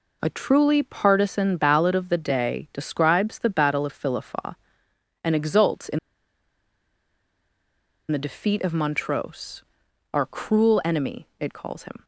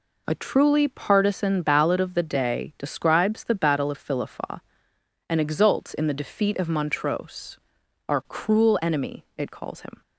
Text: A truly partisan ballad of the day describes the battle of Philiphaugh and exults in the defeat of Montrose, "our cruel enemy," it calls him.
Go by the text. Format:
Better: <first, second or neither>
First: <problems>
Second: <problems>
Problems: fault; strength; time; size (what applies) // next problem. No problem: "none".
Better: second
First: pauses between "in" and "the"; strong; at 5.9 s; 2.1 s long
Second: none